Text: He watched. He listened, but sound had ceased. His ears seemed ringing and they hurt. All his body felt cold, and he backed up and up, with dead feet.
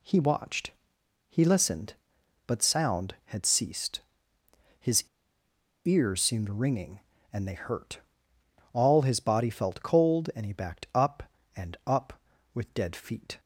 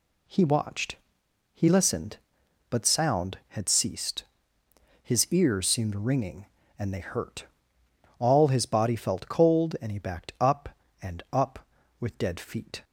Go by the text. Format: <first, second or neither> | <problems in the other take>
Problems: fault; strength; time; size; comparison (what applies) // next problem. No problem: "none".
second | pauses between "His" and "ears"; noticeable; at 5.0 s; 0.81 s long